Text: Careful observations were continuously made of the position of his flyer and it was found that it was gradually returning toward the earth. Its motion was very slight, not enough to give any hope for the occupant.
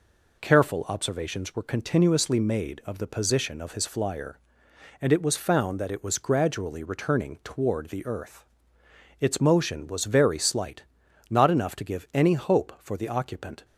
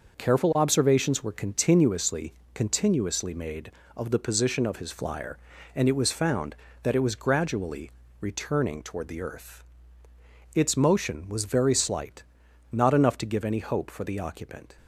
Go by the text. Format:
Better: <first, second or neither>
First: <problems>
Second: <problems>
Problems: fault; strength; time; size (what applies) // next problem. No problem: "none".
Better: first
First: none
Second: says "continuously" twice; at 2.5 s // pauses between "gradually" and "returning"; slight; at 7.9 s; 0.28 s long